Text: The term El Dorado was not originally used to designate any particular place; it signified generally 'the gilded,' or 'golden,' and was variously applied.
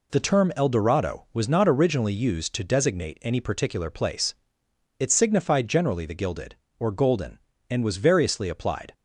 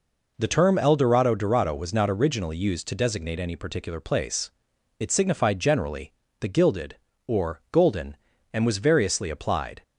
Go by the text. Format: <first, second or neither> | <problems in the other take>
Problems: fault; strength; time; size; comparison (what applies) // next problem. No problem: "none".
first | says "Dorado" twice; at 1.3 s // pauses between "generally" and "the"; slight; at 6.1 s; 0.28 s long